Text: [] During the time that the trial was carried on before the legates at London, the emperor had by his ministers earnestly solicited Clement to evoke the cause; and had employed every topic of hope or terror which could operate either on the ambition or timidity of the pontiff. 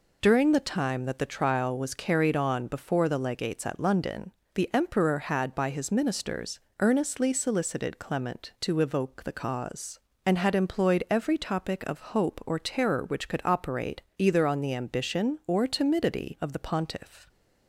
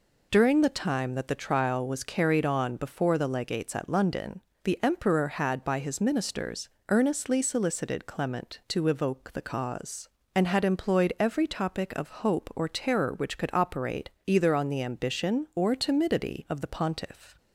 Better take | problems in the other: neither | pauses between "ministers" and "earnestly"; slight; the same in both

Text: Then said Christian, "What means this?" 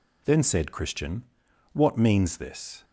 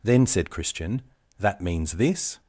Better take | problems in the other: first | says "That" for "What"; at 1.3 s

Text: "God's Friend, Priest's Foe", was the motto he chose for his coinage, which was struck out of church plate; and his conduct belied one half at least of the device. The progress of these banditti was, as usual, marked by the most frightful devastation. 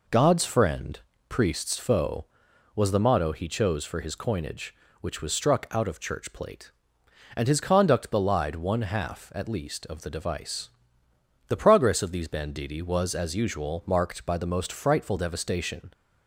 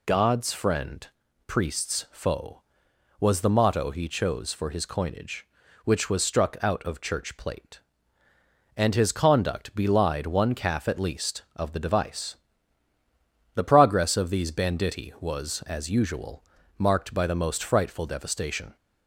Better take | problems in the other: first | says "calf" for "half"; at 10.5 s

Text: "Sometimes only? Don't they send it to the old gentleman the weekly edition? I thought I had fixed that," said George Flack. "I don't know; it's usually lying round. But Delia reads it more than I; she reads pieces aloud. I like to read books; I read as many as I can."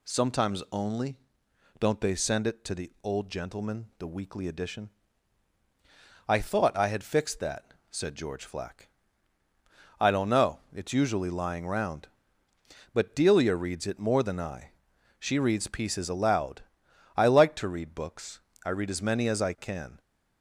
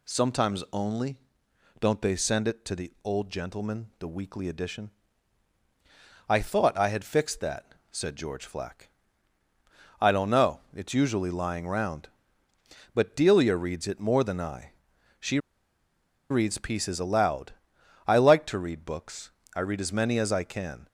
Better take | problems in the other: first | pauses between "she" and "reads"; noticeable; at 15.3 s; 0.92 s long

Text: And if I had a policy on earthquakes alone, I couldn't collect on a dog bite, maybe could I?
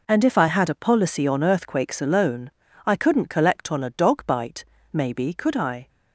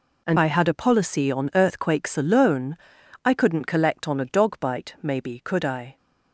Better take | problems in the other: first | skips "if"; at 0.3 s

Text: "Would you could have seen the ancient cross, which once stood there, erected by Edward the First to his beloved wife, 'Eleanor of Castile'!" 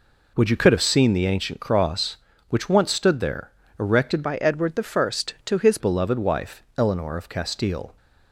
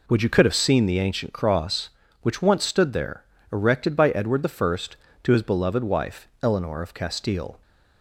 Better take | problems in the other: second | changes voice from "by" to "his"; from 4.2 to 5.7 s; 1.5 s long

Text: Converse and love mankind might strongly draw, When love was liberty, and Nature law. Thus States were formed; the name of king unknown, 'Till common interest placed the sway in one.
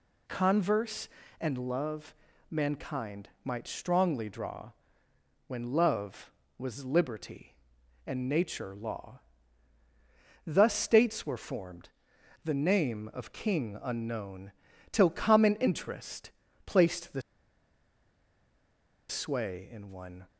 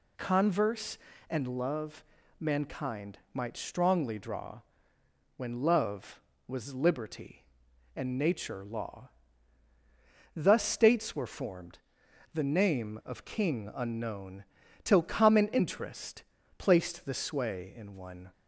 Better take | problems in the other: second | pauses between "love" and "mankind"; at 2.1 s; 0.38 s long; also in the second // pauses between "interest" and "placed"; slight; at 16.3 s; 0.34 s long; slight in the second // pauses between "the" and "sway"; strong; at 17.2 s; 1.8 s long

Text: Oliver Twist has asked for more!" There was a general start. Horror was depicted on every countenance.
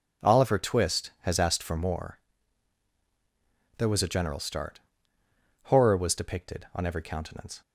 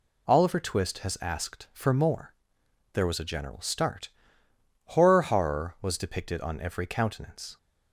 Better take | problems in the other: first | says "Horror" twice; at 5.2 s

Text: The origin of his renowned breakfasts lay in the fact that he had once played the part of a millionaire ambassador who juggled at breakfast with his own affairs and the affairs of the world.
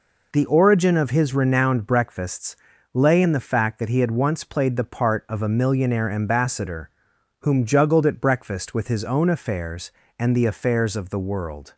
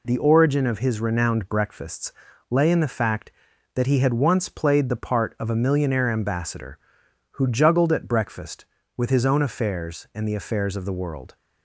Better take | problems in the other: second | pauses between "breakfasts" and "lay"; at 2.5 s; 0.38 s long; slight in the second // says "whom" for "who"; at 7.4 s

